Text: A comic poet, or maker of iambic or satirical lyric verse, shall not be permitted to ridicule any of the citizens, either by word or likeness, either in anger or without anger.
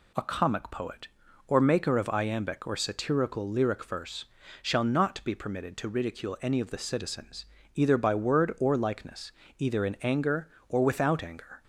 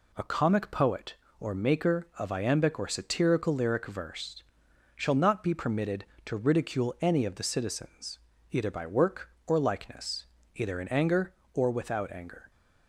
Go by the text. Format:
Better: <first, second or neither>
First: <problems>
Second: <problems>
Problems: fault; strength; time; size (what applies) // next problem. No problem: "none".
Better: first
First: none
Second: says "work" for "word"; at 8.8 s